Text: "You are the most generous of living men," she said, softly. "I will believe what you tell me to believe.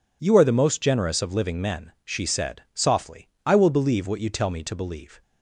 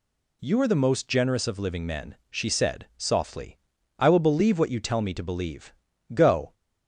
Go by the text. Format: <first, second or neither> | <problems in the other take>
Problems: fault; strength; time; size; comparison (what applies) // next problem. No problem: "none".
first | goes on to say "Go"; slight; from 6.1 s on; 0.40 s long